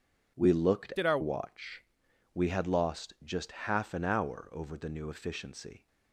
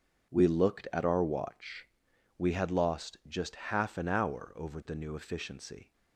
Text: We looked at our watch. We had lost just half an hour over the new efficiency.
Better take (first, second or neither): second